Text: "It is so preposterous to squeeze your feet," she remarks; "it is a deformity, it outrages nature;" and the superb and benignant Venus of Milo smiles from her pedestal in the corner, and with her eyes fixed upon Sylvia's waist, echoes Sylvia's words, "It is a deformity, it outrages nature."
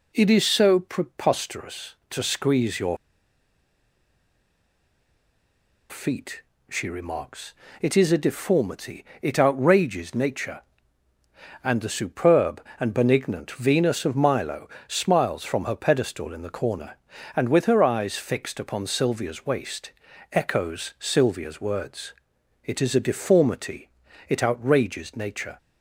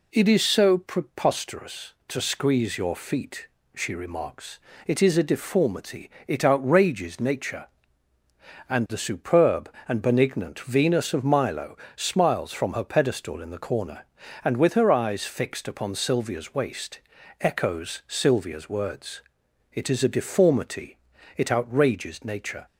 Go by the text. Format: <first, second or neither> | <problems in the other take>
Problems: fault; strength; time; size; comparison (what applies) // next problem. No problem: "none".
second | pauses between "your" and "feet"; strong; at 2.9 s; 2.9 s long // pauses between "Milo" and "smiles"; slight; at 14.6 s; 0.18 s long; slight in the second